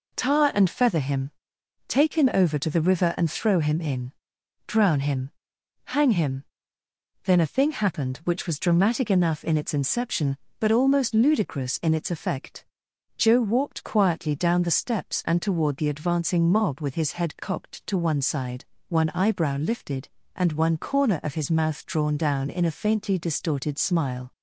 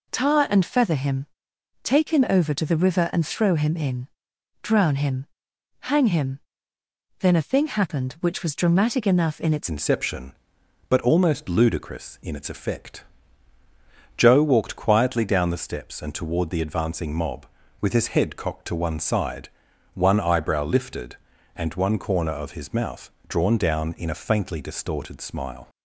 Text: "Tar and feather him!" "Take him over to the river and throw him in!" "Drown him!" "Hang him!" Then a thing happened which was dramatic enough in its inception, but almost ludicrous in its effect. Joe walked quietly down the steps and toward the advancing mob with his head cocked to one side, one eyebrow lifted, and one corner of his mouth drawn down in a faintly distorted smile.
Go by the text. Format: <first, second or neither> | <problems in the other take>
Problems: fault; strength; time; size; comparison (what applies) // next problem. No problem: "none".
first | changes voice at "inception"; from 9.6 s on; 16.0 s long // pauses between "mouth" and "drawn"; slight; at 23.0 s; 0.18 s long